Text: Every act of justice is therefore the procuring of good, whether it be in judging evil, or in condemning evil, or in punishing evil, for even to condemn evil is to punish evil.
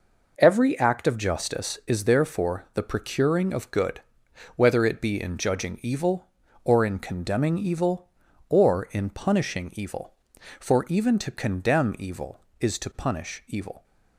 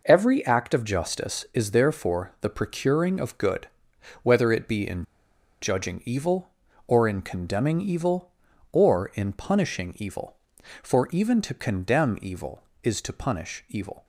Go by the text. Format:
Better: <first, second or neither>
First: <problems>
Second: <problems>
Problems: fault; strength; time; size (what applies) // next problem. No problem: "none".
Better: first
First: none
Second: pauses between "in" and "judging"; noticeable; at 5.0 s; 0.56 s long